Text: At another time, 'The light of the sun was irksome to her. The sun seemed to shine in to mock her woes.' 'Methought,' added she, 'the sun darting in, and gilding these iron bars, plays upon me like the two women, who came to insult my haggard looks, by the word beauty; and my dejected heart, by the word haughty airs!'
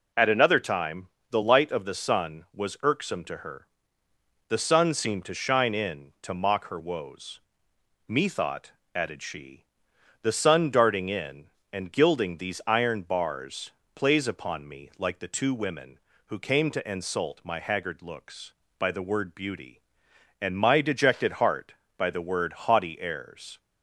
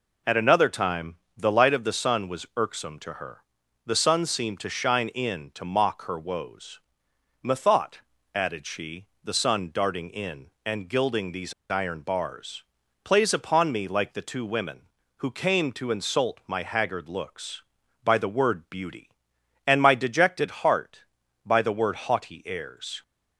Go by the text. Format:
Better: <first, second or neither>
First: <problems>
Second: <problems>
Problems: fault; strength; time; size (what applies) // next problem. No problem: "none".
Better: first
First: none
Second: pauses between "these" and "iron"; slight; at 11.5 s; 0.18 s long